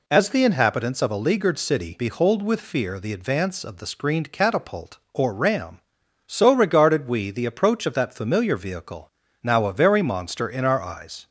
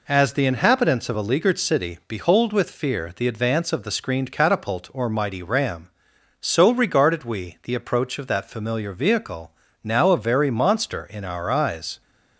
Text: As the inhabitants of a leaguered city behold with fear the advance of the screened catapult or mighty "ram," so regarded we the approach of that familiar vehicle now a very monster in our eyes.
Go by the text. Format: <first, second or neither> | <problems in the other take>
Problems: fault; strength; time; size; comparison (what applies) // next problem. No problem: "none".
second | skips "mighty"; at 5.3 s // pauses between "vehicle" and "now"; slight; at 9.1 s; 0.32 s long; slight in the second